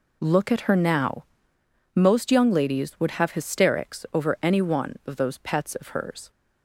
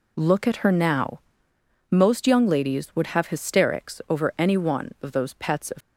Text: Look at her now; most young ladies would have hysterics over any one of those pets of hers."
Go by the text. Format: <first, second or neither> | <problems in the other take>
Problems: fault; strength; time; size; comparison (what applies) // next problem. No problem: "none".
first | stops before "hers"; at 5.8 s